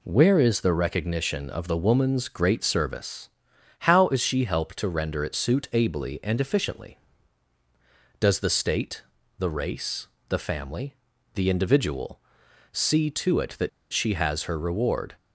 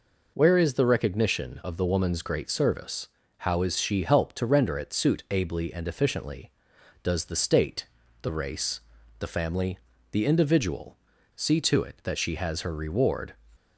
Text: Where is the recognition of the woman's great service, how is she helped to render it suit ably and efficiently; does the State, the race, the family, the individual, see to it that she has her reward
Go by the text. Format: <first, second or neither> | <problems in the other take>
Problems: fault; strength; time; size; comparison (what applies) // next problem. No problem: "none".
second | pauses between "that" and "she"; slight; at 13.6 s; 0.22 s long